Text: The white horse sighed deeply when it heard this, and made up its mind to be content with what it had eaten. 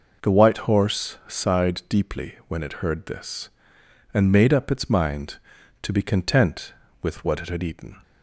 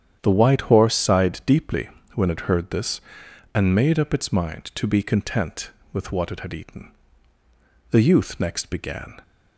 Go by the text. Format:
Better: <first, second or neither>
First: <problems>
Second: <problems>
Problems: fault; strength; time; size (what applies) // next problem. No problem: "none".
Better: first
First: none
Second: starts louder than the rest; strong; until 1.2 s; 9 dB // pauses between "deeply" and "when"; slight; at 1.8 s; 0.28 s long // goes on to say "The youth next began"; noticeable; from 7.9 s on; 1.3 s long